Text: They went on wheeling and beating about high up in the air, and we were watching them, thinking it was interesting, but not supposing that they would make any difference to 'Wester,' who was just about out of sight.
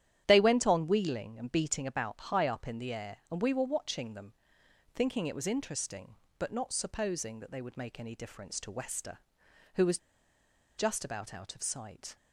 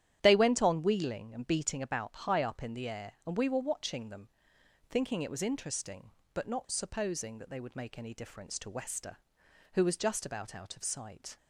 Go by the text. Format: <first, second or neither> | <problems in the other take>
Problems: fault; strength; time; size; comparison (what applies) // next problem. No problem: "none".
second | starts louder than the rest; strong; until 1.2 s; 11 dB; strong in the second // pauses between "was" and "just"; noticeable; at 9.9 s; 0.79 s long